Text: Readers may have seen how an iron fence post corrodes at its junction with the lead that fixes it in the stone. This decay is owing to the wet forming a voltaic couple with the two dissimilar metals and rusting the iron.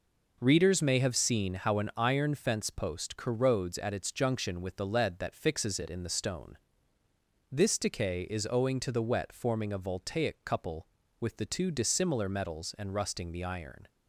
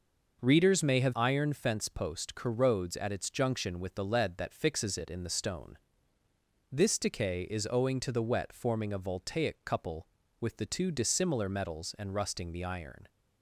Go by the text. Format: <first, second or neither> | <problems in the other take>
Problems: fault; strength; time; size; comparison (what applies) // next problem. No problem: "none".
first | skips "seen how an"; at 1.1 s